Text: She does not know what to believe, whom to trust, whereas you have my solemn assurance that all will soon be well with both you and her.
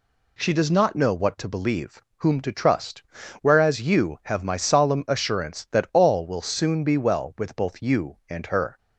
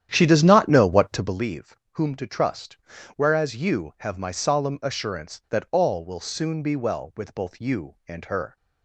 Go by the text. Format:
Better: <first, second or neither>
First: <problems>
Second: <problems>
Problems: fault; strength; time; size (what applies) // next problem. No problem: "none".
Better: first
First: none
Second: starts louder than the rest; strong; until 1.5 s; 10 dB